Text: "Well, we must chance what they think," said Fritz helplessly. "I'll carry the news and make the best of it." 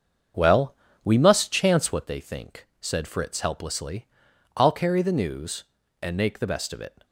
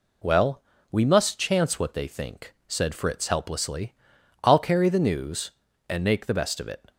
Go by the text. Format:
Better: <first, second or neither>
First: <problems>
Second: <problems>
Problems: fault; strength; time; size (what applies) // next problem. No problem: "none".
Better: second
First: starts louder than the rest; until 2.0 s; 7 dB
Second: none